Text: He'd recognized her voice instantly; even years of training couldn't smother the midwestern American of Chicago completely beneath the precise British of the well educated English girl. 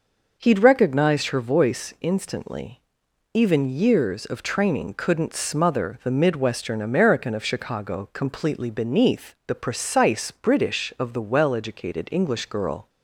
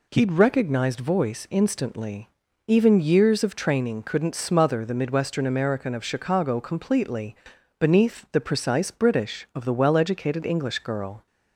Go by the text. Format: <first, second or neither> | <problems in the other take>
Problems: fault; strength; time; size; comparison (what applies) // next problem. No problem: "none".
first | skips "her"; at 0.9 s // pauses between "completely" and "beneath"; at 7.3 s; 0.44 s long